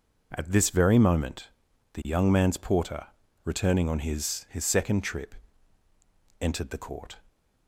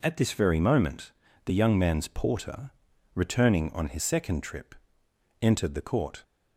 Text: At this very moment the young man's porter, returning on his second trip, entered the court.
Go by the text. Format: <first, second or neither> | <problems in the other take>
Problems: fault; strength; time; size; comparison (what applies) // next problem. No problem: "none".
second | pauses between "moment" and "the"; at 1.4 s; 0.42 s long; slight in the second // says "his" twice; at 4.5 s